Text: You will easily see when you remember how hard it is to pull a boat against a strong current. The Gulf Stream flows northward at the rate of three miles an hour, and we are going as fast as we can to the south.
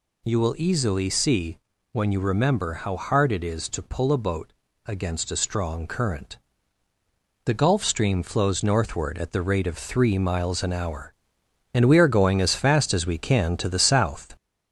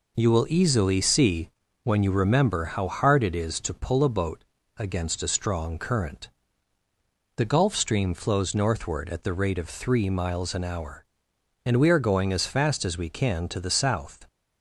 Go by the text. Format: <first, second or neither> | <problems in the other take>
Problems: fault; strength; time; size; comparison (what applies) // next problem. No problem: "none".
second | gets louder; slight; throughout; 3.5 dB // pauses between "see" and "when"; slight; at 1.5 s; 0.34 s long; slight in the second // pauses between "boat" and "against"; slight; at 4.5 s; 0.32 s long; slight in the second